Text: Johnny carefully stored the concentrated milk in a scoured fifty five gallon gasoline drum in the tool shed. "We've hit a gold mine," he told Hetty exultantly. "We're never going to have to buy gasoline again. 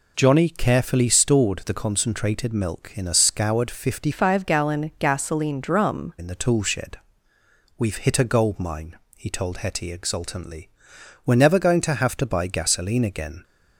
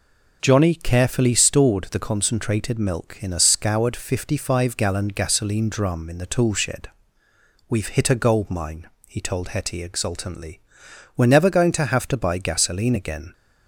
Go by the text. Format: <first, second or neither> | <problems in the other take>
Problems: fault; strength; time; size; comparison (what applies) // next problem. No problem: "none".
second | changes voice from "five" to "drum"; from 4.1 to 6.1 s; 2.0 s long